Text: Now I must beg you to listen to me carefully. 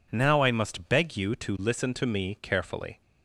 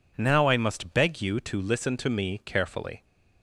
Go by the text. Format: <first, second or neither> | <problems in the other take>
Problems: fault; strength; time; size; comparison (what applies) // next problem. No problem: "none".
neither | none